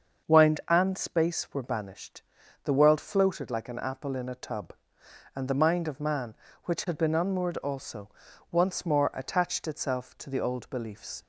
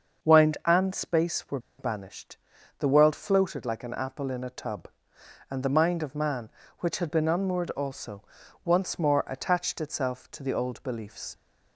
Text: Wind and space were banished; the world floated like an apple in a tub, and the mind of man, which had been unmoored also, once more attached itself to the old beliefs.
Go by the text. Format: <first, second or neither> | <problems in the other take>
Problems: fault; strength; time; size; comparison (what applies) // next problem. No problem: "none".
first | starts louder than the rest; until 1.3 s; 6.5 dB; also in the first // pauses between "were" and "banished"; slight; at 1.5 s; 0.20 s long